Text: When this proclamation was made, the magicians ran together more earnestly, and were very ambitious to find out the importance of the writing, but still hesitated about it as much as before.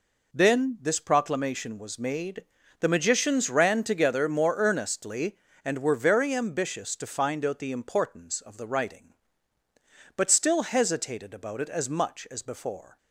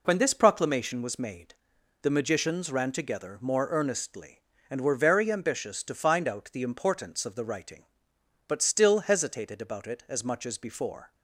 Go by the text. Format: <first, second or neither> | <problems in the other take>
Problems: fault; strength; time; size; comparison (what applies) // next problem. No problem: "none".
second | says "Then" for "When"; at 0.3 s